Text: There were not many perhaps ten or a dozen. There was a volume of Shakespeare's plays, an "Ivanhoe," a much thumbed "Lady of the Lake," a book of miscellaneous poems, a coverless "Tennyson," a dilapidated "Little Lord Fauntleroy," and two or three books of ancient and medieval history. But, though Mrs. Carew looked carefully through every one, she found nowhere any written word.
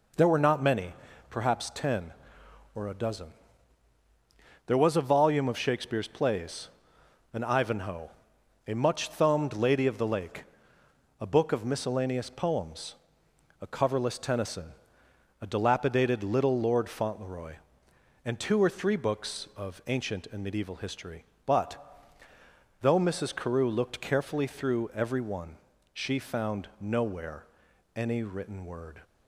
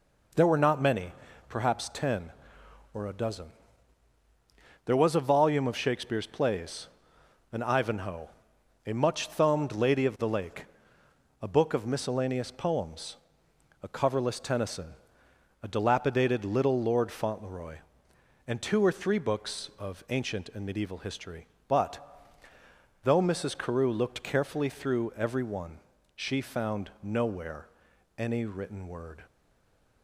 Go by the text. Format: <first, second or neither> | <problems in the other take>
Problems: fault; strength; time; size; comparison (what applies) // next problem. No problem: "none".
first | pauses between "many" and "perhaps"; slight; at 1.1 s; 0.36 s long; slight in the first // pauses between "nowhere" and "any"; noticeable; at 27.6 s; 0.50 s long; noticeable in the first // stays silent after the last word; slight; from 29.2 s on; 0.8 s long